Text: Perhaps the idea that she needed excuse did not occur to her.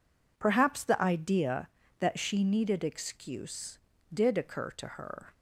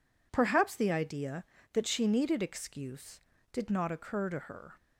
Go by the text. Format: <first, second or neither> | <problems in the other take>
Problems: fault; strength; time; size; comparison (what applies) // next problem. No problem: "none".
second | skips "not"; at 4.3 s